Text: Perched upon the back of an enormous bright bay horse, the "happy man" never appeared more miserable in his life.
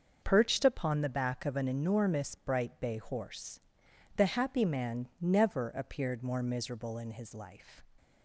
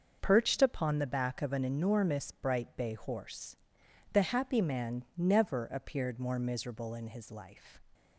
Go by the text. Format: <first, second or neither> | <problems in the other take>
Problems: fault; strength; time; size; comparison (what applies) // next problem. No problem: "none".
neither | starts louder than the rest; the same in both